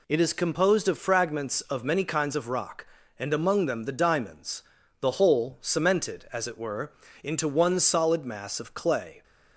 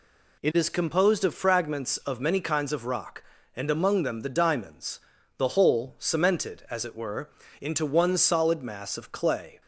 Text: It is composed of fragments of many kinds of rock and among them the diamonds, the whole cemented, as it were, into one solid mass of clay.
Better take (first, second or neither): neither